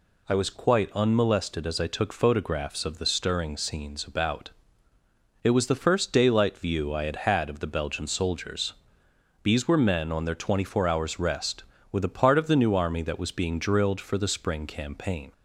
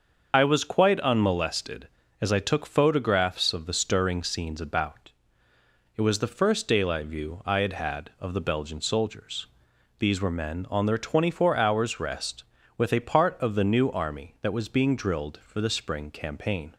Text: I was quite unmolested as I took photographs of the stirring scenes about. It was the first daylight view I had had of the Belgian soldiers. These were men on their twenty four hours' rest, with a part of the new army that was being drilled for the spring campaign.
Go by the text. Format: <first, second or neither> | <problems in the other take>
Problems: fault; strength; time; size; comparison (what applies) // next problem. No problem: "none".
first | loses the start of "I"; at 0.3 s; 50 ms // starts louder than the rest; until 1.3 s; 6.5 dB